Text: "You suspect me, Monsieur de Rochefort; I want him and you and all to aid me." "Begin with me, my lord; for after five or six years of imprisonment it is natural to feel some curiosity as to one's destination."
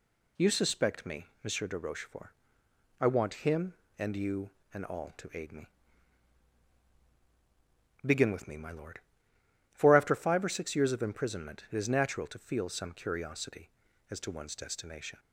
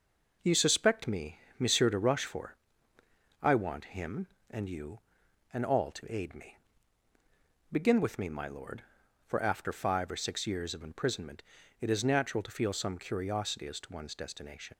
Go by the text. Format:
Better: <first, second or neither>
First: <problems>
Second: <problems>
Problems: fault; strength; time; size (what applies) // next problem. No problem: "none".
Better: first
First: none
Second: pauses between "imprisonment" and "it"; at 11.4 s; 0.38 s long // leaves "destination" unfinished; at 14.7 s; 45 ms